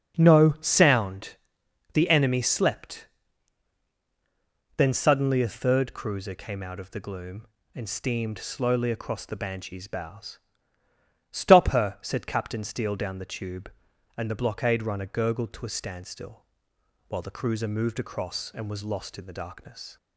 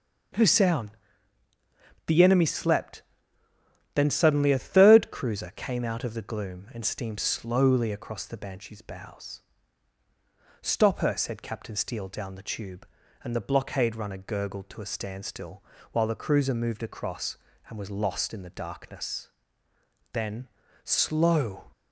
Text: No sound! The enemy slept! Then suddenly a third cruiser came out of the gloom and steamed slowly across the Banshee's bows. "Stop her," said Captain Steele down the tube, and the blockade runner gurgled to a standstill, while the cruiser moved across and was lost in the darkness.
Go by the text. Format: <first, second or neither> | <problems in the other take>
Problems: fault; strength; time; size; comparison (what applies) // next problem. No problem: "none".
first | starts louder than the rest; until 2.5 s; 6.5 dB; also in the first // goes on to say "Then Slow"; from 20.1 s on; 1.5 s long